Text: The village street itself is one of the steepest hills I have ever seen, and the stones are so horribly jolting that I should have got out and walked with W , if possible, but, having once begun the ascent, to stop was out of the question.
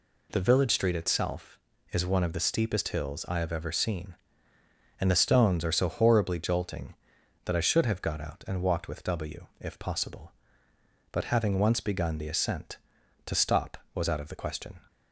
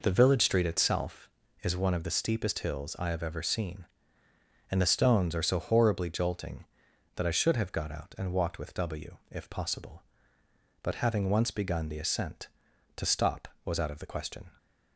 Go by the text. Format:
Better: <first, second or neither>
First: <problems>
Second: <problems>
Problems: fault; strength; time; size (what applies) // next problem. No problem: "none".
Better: first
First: none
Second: starts louder than the rest; noticeable; until 1.7 s; 4.5 dB